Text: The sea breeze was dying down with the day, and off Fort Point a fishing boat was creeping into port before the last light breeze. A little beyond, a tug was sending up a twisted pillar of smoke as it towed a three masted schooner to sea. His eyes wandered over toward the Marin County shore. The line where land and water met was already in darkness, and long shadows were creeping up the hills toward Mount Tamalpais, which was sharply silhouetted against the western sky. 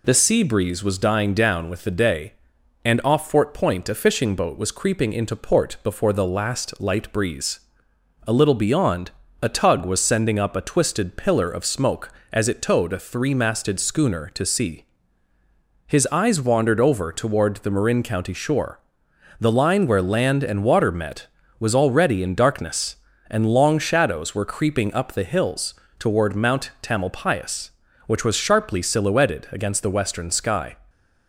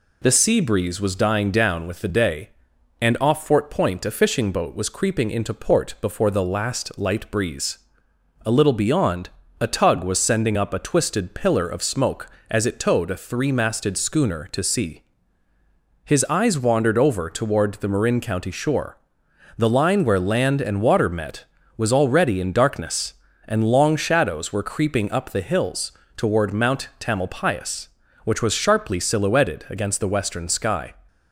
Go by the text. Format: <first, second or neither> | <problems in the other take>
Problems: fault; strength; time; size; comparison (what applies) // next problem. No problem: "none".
neither | pauses between "hills" and "toward"; slight; the same in both